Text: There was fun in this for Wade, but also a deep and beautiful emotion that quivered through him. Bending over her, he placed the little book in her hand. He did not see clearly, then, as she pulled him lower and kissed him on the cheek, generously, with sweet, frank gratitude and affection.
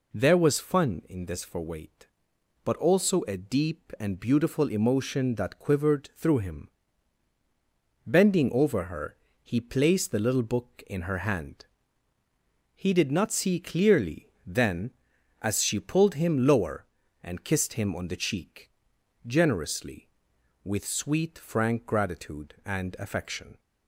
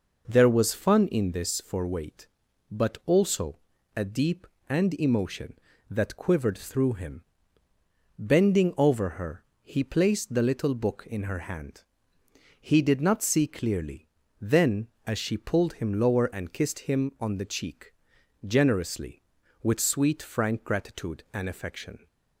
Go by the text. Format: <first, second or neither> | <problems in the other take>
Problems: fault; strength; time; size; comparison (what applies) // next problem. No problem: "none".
first | pauses between "also" and "a"; slight; at 3.5 s; 0.36 s long // skips "beautiful"; at 4.9 s